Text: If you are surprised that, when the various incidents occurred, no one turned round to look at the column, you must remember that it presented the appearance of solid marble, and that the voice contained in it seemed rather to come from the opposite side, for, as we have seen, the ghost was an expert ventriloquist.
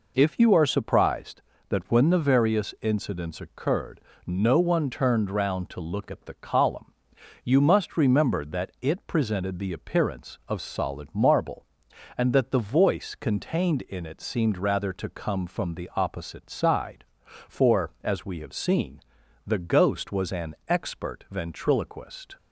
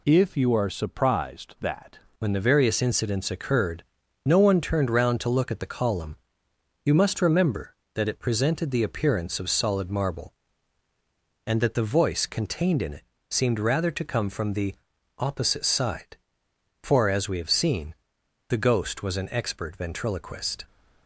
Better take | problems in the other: first | changes voice at "when"; from 2.1 s on; 18.5 s long // pauses between "it" and "seemed"; slight; at 13.0 s; 0.26 s long // pauses between "the" and "opposite"; at 14.7 s; 0.44 s long

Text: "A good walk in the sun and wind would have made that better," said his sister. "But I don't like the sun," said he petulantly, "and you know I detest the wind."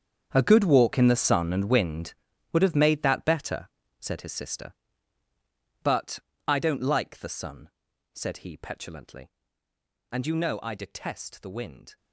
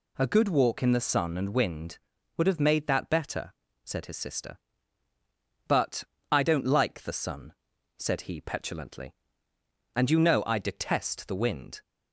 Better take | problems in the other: second | gets quieter; strong; throughout; 16 dB // pauses between "But" and "I"; slight; at 6.1 s; 0.28 s long; slight in the second

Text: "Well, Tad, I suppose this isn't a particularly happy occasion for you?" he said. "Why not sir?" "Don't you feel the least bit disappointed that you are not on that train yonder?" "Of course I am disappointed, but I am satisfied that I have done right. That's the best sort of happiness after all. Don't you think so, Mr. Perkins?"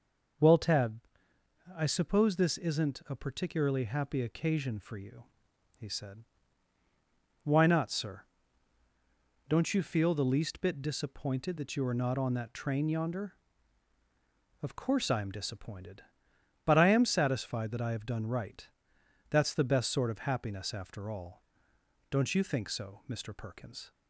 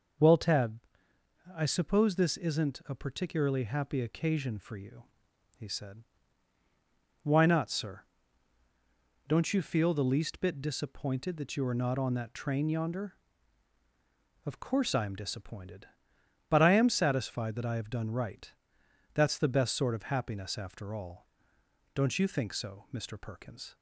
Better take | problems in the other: neither | none

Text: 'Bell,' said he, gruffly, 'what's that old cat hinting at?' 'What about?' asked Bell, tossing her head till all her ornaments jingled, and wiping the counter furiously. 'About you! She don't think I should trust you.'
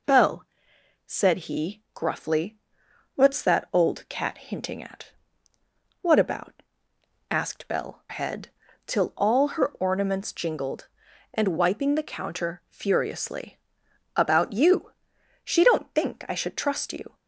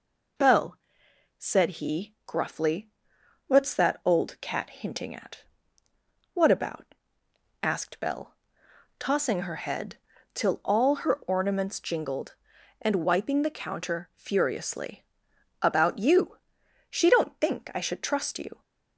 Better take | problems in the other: second | skips "tossing her"; at 8.0 s // pauses between "head" and "till"; at 8.4 s; 0.38 s long; also in the second

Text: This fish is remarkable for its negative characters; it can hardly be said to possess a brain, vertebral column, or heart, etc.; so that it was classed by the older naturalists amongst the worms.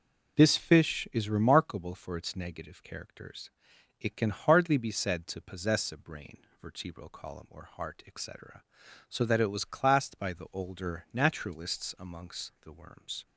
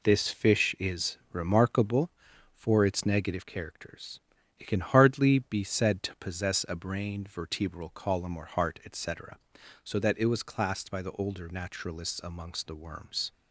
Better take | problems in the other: neither | none

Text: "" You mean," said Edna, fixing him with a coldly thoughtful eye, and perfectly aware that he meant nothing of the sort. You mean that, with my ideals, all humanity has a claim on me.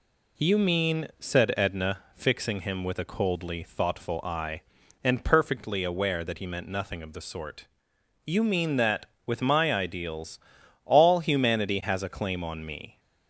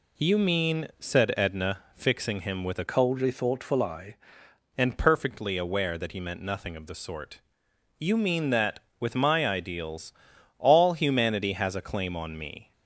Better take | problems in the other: first | changes voice from "coldly" to "eye"; from 2.8 to 4.1 s; 1.3 s long

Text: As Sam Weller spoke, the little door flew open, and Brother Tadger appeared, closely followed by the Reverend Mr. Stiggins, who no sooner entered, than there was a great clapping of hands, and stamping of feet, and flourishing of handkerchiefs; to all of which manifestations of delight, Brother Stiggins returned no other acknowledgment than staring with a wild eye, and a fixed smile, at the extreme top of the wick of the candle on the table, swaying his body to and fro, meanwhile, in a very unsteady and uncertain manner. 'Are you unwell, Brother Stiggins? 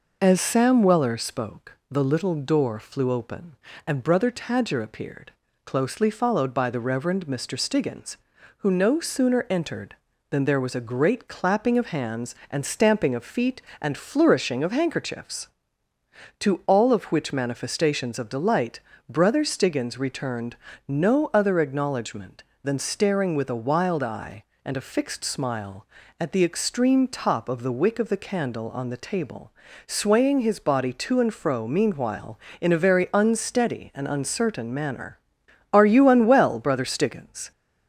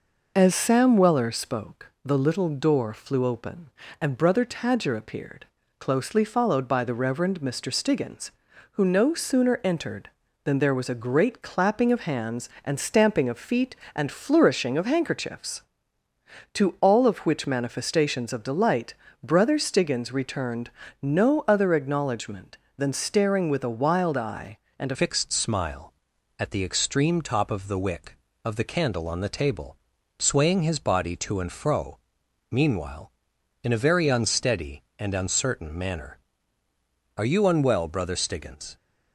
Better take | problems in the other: first | pauses between "returned" and "no"; slight; at 20.6 s; 0.32 s long; slight in the first // changes voice at "fixed"; from 24.9 s on; 13.8 s long

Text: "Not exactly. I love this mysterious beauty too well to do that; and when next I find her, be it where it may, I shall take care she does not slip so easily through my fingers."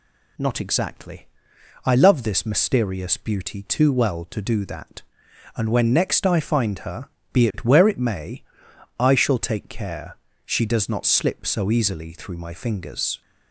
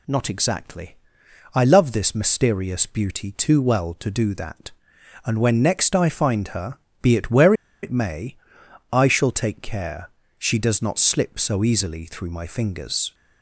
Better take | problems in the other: first | pauses between "where" and "it"; slight; at 7.5 s; 0.30 s long // pauses between "care" and "she"; slight; at 10.0 s; 0.28 s long; slight in the first

